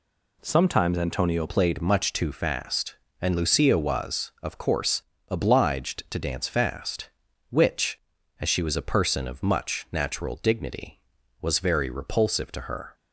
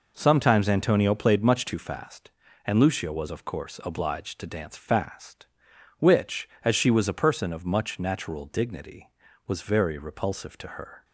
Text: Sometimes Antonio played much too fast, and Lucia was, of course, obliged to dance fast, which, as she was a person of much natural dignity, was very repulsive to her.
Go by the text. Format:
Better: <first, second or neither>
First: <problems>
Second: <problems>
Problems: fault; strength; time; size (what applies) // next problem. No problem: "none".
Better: second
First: changes voice at "played"; from 1.4 s on; 11.5 s long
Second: none